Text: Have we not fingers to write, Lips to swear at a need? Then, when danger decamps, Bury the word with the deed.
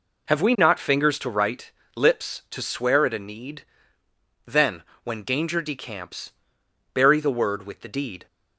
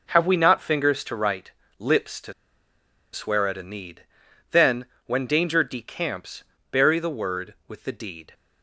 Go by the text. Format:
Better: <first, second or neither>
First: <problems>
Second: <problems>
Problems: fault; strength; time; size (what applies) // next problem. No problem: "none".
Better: first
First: none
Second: pauses between "to" and "swear"; noticeable; at 2.3 s; 0.80 s long